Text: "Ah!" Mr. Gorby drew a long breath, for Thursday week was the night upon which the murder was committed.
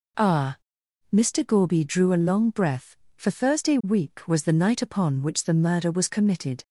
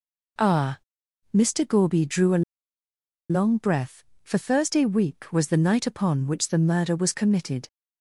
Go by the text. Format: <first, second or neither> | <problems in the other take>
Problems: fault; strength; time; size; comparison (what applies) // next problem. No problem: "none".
first | pauses between "a" and "long"; noticeable; at 2.4 s; 0.88 s long